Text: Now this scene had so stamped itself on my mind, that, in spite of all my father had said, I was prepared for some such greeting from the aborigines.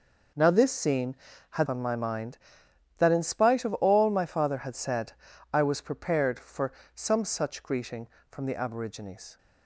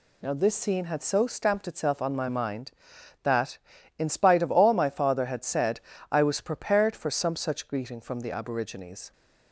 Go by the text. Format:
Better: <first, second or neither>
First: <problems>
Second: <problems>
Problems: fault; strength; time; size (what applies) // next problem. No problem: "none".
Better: second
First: skips "so stamped itself"; at 1.6 s // pauses between "for" and "some"; slight; at 6.7 s; 0.22 s long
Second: none